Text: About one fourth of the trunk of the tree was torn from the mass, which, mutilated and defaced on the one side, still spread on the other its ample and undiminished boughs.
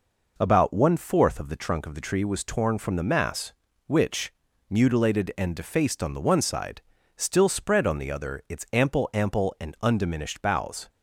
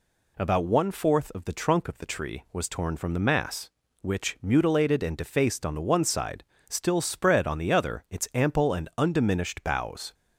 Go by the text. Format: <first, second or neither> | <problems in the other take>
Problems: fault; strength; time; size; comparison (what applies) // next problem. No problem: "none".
second | says "ample" twice; at 9.1 s